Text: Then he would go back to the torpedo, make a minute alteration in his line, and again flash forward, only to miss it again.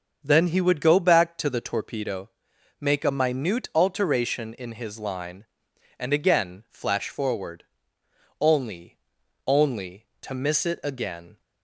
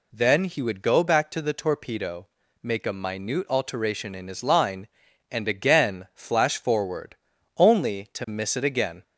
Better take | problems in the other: second | starts louder than the rest; until 1.2 s; 6.5 dB // says "only" twice; at 9.4 s

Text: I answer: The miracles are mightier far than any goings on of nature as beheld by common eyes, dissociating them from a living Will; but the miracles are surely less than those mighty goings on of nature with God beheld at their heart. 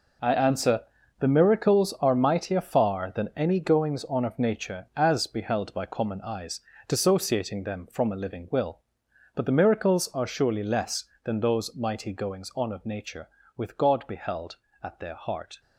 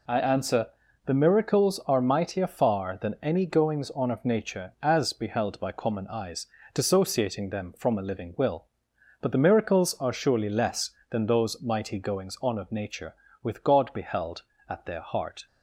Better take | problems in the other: second | gets quieter; strong; throughout; 11.5 dB

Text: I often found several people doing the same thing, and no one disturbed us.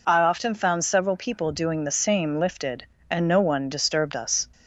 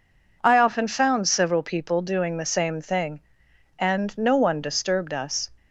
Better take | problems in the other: second | says "lifted" for "thing"; at 2.3 s

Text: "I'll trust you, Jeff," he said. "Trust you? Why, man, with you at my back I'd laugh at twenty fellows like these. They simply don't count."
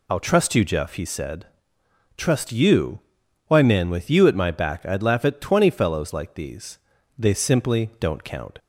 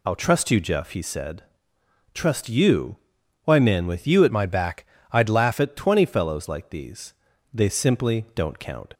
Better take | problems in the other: first | changes voice from "my" to "laugh"; from 4.2 to 5.5 s; 1.3 s long // pauses between "back" and "I'd"; slight; at 4.8 s; 0.24 s long

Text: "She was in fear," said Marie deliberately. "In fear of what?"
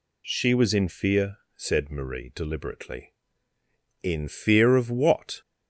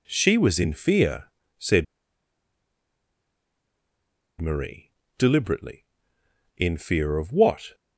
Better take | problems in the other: first | pauses between "said" and "Marie"; strong; at 1.8 s; 2.5 s long // pauses between "Marie" and "deliberately"; slight; at 4.9 s; 0.26 s long

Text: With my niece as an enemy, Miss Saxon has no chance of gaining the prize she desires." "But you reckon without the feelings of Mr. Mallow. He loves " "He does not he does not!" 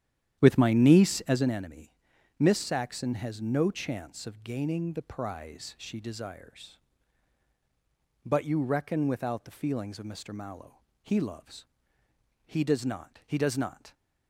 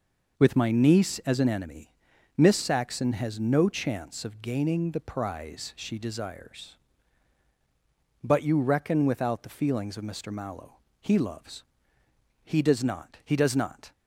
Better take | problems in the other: second | starts louder than the rest; strong; until 1.5 s; 10.5 dB

